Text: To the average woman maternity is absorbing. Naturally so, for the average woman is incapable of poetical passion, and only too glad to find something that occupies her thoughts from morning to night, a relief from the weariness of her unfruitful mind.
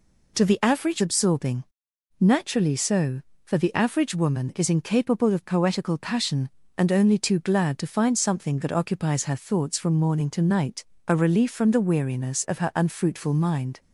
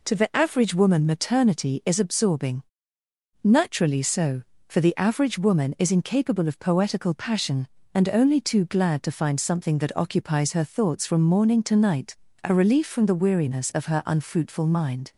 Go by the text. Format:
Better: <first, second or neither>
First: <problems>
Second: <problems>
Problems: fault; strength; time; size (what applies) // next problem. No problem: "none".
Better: second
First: skips "woman maternity is"; at 1.0 s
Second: none